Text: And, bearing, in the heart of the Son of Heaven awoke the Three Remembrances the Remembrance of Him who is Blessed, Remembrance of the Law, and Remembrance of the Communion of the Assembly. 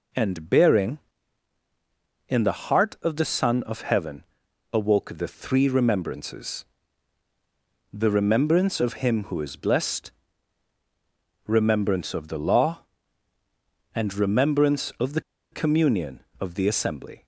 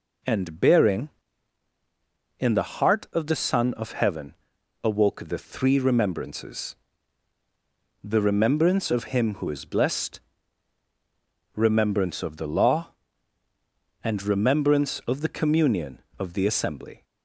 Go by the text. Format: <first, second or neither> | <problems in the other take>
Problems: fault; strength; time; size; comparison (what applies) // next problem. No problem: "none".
second | pauses between "Heaven" and "awoke"; noticeable; at 4.2 s; 0.48 s long; noticeable in the second // pauses between "Remembrances" and "the"; strong; at 6.6 s; 1.2 s long; strong in the second // pauses between "the" and "Communion"; slight; at 15.1 s; 0.31 s long